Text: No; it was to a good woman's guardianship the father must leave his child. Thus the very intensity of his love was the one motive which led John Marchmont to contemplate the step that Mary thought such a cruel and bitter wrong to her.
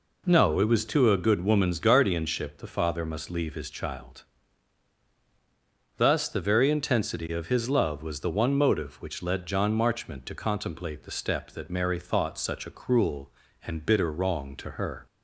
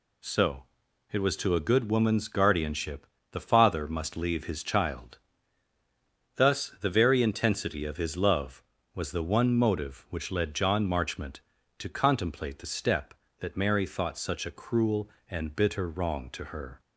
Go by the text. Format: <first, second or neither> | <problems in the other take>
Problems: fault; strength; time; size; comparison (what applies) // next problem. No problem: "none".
first | says "So" for "No"; at 0.2 s // pauses between "guardianship" and "the"; slight; at 3.0 s; 0.26 s long